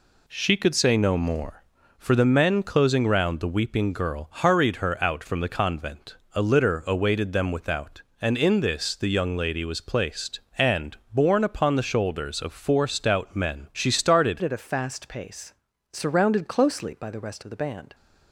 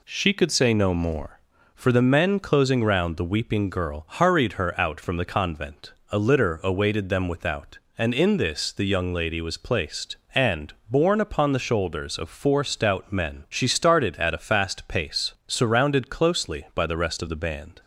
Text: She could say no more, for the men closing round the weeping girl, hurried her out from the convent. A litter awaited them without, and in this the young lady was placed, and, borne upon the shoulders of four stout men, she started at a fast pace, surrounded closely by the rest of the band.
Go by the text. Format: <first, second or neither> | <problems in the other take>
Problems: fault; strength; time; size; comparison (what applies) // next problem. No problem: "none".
second | changes voice at "at"; from 14.4 s on; 3.5 s long